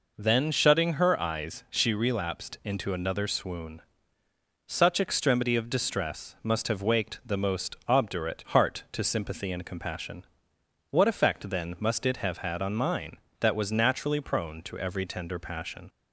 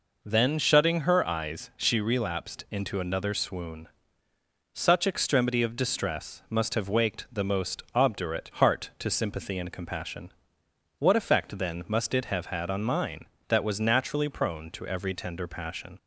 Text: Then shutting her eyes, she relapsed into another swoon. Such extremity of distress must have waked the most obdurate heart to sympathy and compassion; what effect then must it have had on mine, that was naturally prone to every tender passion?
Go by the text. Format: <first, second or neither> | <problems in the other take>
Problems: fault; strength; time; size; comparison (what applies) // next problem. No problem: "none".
neither | none